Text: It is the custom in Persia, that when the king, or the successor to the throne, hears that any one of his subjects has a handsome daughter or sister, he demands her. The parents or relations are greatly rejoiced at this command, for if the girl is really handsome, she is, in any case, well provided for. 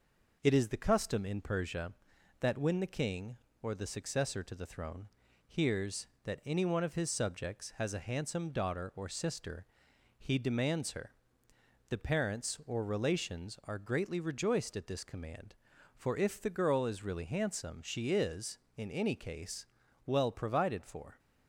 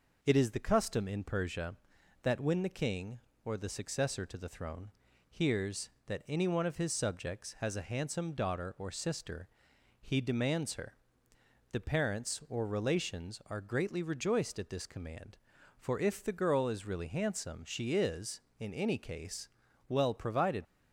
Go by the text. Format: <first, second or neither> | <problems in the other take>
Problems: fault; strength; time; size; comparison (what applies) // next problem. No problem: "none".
first | stops before "for"; at 20.6 s